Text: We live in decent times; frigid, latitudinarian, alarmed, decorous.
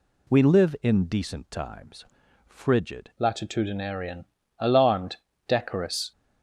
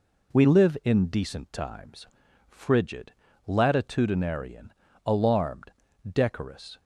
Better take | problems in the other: second | changes voice at "latitudinarian"; from 3.1 s on; 3.0 s long

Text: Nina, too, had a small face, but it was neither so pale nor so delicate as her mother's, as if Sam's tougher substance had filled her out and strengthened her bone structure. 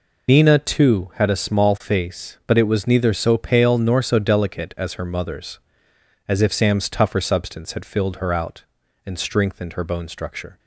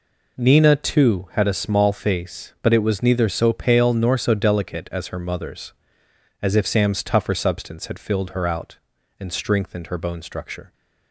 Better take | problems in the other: second | loses the start of "Nina"; at 0.2 s; 80 ms

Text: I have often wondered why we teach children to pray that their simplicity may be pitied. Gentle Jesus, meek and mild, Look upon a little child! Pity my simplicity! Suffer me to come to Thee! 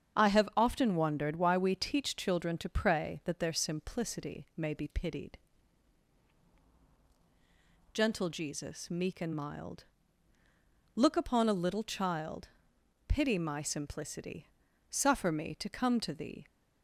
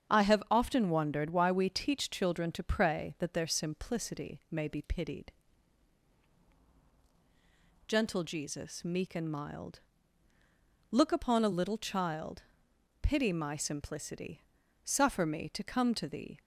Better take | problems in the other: neither | starts louder than the rest; strong; the same in both

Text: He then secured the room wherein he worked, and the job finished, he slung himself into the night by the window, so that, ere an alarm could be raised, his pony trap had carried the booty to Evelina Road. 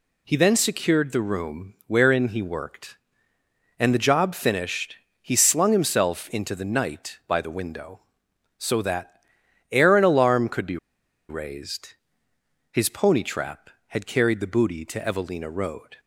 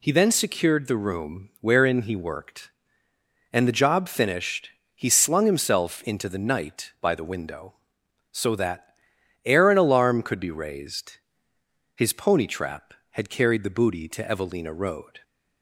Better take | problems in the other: second | pauses between "be" and "raised"; noticeable; at 10.7 s; 0.52 s long

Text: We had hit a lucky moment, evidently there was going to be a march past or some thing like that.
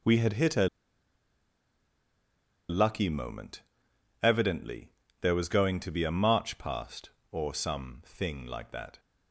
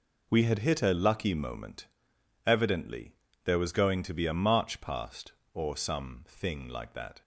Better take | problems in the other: second | pauses between "a" and "lucky"; strong; at 0.6 s; 2.0 s long // pauses between "evidently" and "there"; slight; at 4.8 s; 0.32 s long; slight in the second

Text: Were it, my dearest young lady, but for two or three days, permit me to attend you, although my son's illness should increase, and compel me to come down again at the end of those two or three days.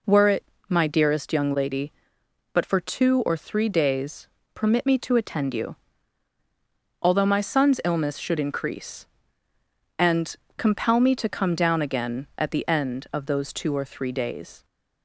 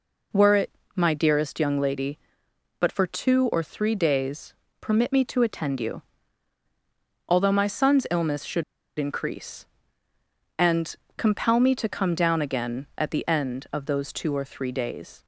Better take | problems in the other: first | pauses between "should" and "increase"; slight; at 8.6 s; 0.34 s long // pauses between "and" and "compel"; slight; at 10.9 s; 0.24 s long; slight in the first

